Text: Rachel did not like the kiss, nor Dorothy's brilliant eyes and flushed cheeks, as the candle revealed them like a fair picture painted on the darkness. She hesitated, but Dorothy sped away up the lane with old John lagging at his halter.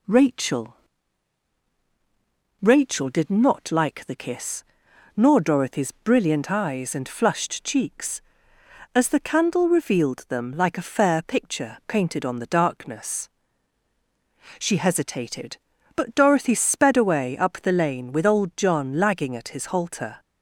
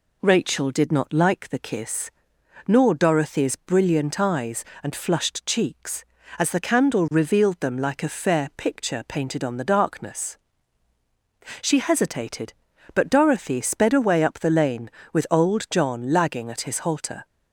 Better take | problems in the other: second | says "Rachel" twice; at 2.6 s

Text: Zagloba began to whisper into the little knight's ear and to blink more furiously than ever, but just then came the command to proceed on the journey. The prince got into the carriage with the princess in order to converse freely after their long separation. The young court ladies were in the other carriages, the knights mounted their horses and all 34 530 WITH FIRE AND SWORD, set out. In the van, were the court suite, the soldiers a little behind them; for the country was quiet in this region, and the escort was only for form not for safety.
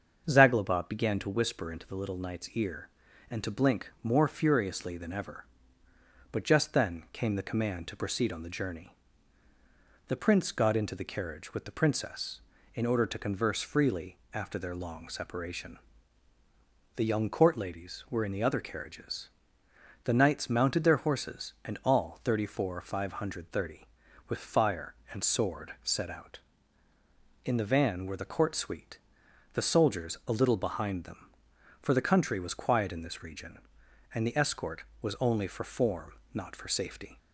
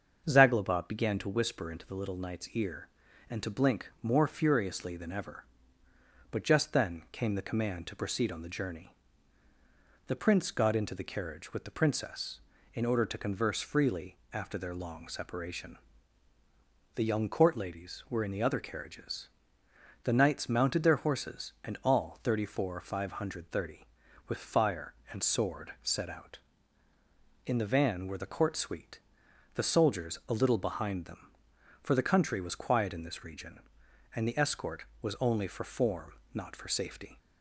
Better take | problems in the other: neither | starts louder than the rest; the same in both // pauses between "freely" and "after"; slight; the same in both // pauses between "form" and "not"; slight; the same in both

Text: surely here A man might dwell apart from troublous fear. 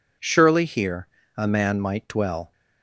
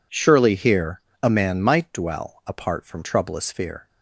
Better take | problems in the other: second | pauses between "here" and "A"; slight; at 1.0 s; 0.30 s long; slight in the second // stops before "apart from troublous fear"; at 2.5 s

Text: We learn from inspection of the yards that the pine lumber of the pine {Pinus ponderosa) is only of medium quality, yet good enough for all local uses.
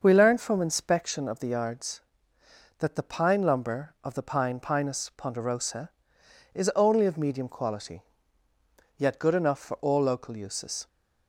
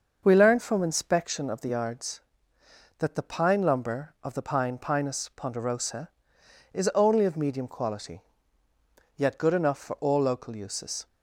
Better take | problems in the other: neither | starts louder than the rest; the same in both

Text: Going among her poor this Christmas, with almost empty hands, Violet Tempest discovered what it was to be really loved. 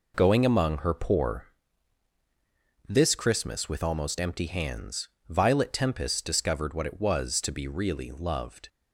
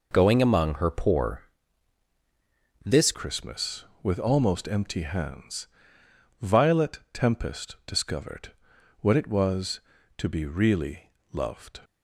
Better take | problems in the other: first | pauses between "poor" and "this"; strong; at 1.3 s; 1.4 s long; strong in the first // changes voice at "Christmas"; from 3.1 s on; 8.7 s long // pauses between "discovered" and "what"; noticeable; at 8.5 s; 0.48 s long // pauses between "really" and "loved"; slight; at 11.1 s; 0.20 s long

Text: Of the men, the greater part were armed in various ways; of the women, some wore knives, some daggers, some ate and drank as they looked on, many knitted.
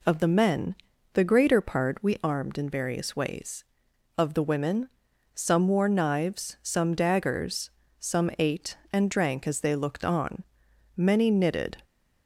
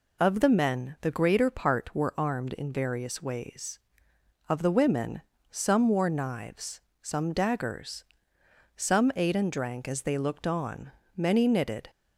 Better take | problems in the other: second | says "we" for "were"; at 2.0 s

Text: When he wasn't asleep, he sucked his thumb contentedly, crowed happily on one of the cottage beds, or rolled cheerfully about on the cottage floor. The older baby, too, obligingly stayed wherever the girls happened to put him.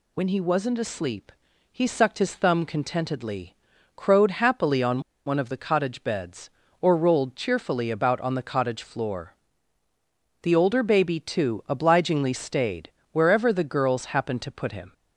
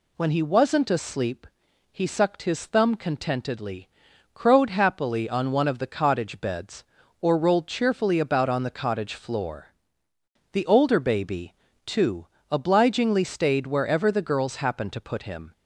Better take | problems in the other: second | pauses between "on" and "one"; slight; at 5.0 s; 0.25 s long // pauses between "stayed" and "wherever"; slight; at 12.9 s; 0.22 s long

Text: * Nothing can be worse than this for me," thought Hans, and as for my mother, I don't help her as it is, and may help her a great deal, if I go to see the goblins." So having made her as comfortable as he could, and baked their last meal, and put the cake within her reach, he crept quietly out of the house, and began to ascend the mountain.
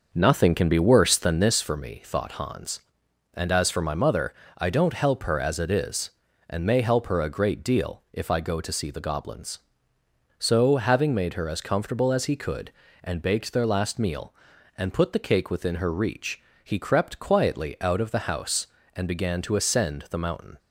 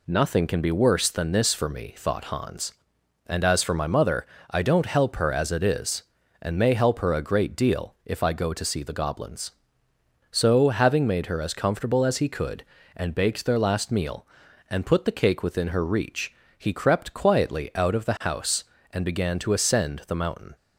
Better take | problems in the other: second | starts louder than the rest; noticeable; until 1.6 s; 6 dB

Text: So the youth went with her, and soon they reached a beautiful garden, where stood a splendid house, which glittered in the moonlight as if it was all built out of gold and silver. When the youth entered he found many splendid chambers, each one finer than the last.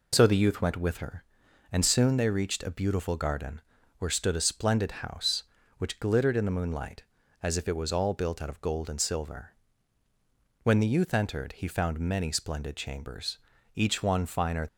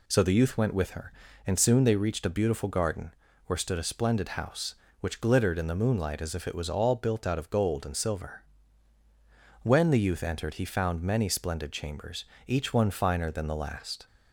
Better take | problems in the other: second | stops before "than the last"; at 14.6 s

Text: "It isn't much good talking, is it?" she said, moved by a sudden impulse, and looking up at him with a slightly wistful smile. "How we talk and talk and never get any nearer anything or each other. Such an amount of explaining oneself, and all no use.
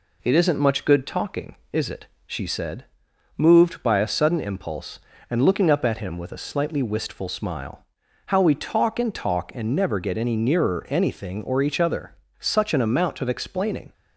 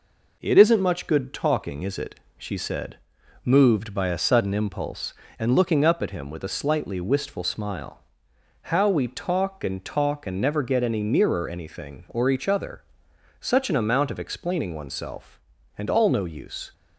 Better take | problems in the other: second | stops before "oneself and all no use"; at 13.9 s

